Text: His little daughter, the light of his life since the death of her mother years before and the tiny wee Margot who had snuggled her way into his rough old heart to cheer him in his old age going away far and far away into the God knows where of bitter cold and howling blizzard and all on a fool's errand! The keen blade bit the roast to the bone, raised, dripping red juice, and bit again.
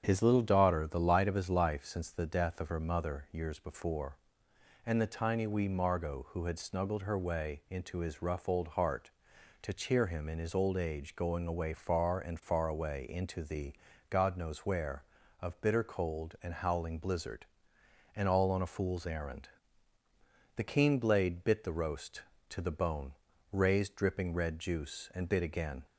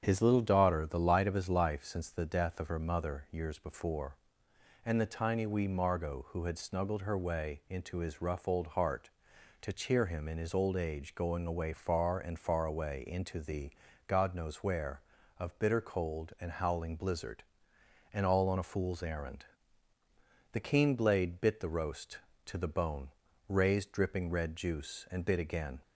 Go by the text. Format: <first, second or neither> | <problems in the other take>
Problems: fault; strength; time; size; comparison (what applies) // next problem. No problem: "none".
neither | starts louder than the rest; strong; the same in both // pauses between "the" and "God"; slight; the same in both